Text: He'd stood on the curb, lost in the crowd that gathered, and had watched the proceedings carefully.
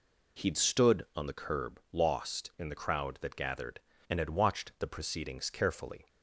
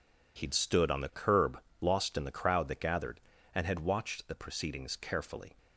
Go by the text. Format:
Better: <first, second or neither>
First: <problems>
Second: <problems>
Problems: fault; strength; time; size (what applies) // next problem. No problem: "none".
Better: neither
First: none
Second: none